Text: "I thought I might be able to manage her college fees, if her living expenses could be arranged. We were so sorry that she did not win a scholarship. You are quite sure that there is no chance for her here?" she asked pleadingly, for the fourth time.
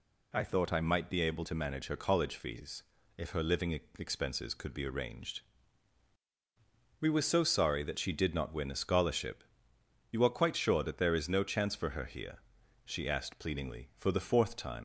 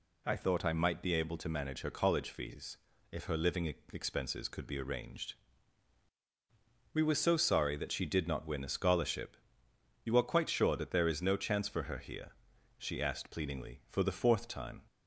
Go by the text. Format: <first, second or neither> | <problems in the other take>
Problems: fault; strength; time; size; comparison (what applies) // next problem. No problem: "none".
second | pauses between "living" and "expenses"; slight; at 3.7 s; 0.26 s long; slight in the second // leaves "time" unfinished; at 14.7 s; 110 ms